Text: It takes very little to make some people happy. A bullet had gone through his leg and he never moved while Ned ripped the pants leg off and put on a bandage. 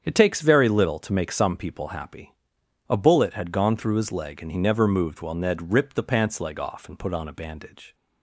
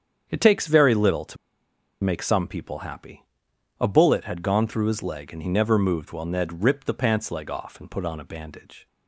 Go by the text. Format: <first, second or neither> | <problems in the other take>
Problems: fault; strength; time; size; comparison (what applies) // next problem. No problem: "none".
first | starts louder than the rest; strong; until 1.3 s; 7.5 dB; strong in the first // pauses between "to" and "make"; noticeable; at 1.3 s; 0.67 s long